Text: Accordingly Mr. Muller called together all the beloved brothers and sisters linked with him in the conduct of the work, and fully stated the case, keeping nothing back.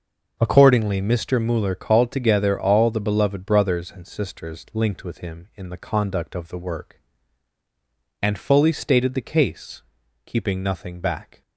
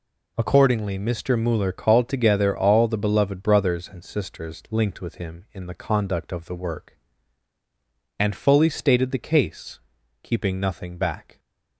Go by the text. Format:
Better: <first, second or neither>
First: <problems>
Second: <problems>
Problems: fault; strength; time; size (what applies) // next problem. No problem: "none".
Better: second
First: starts louder than the rest; noticeable; until 1.4 s; 6 dB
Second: none